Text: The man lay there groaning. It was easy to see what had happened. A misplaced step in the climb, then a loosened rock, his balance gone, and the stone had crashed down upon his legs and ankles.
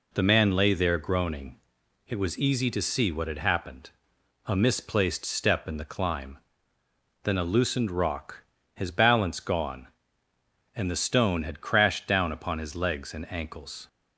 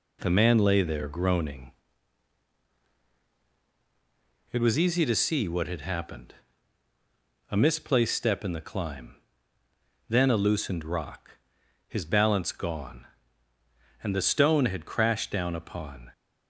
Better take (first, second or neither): first